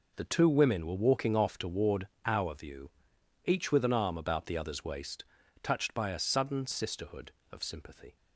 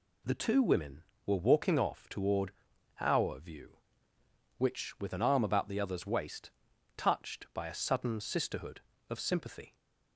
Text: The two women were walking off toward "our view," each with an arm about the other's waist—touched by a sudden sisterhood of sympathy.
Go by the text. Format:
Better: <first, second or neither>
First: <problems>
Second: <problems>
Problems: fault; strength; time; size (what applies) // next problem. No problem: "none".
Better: first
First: pauses between "toward" and "our"; slight; at 2.0 s; 0.16 s long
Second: pauses between "toward" and "our"; noticeable; at 2.5 s; 0.50 s long // says "which" for "each"; at 4.5 s